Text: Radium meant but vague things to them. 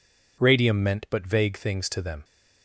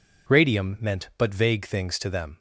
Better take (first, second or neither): neither